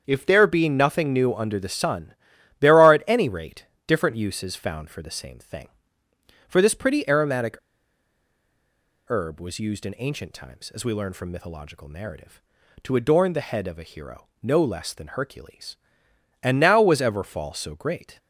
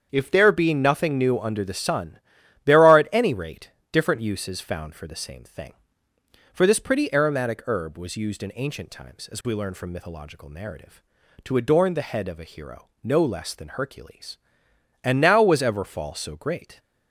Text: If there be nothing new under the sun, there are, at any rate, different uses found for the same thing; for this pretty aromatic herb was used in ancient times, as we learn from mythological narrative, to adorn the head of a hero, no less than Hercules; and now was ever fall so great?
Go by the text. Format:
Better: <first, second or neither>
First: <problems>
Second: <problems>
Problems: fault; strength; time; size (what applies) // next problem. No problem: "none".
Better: second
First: starts louder than the rest; strong; until 1.0 s; 7.5 dB // pauses between "aromatic" and "herb"; strong; at 7.5 s; 1.5 s long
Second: starts louder than the rest; strong; until 1.1 s; 7.5 dB